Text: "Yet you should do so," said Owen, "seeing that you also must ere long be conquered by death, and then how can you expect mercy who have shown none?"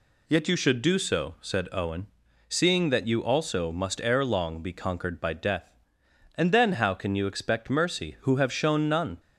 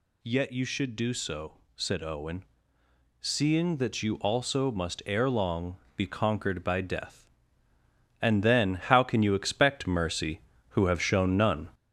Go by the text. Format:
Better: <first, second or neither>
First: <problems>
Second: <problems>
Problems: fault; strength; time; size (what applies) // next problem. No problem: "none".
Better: first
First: none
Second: gets louder; noticeable; throughout; 4 dB // pauses between "long" and "be"; slight; at 5.7 s; 0.18 s long